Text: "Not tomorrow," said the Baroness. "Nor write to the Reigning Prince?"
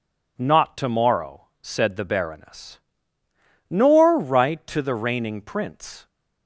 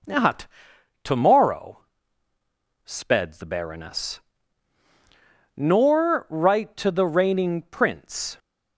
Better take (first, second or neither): first